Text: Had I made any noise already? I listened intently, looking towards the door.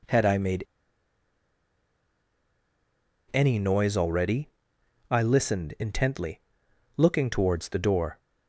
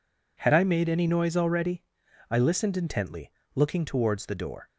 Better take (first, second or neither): second